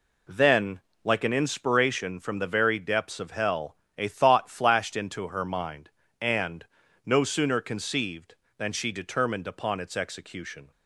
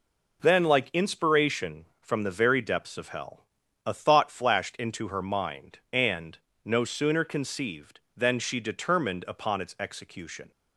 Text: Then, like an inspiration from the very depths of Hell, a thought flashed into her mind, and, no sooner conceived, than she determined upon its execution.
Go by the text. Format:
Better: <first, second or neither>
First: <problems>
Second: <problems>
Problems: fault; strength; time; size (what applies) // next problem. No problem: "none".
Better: first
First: none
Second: skips "an"; at 0.9 s